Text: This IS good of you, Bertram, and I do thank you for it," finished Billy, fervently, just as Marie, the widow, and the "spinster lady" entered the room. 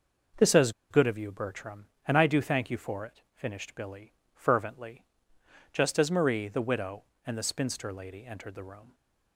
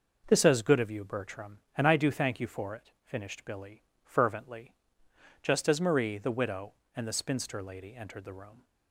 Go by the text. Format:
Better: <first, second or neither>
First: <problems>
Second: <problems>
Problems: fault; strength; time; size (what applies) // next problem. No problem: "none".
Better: second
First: pauses between "IS" and "good"; slight; at 0.7 s; 0.19 s long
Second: none